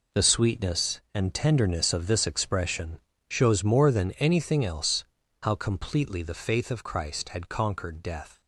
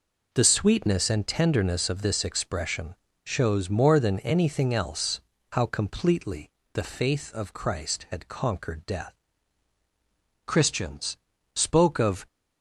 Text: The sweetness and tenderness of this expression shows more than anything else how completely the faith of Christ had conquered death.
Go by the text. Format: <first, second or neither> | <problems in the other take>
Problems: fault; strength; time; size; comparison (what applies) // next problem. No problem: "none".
first | pauses between "expression" and "shows"; slight; at 2.9 s; 0.26 s long; slight in the first // pauses between "else" and "how"; slight; at 5.1 s; 0.32 s long; also in the first // pauses between "completely" and "the"; slight; at 6.4 s; 0.22 s long // goes on to say "Christians spoke of"; strong; from 10.4 s on; 1.8 s long